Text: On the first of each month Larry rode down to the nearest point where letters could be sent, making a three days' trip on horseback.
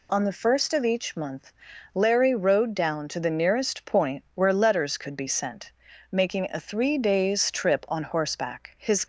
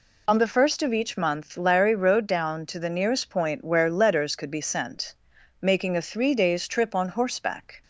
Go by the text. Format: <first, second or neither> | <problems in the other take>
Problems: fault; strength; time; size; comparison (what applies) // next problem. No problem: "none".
second | pauses between "month" and "Larry"; at 1.5 s; 0.42 s long // goes on to say "His"; slight; from 8.7 s on; 0.26 s long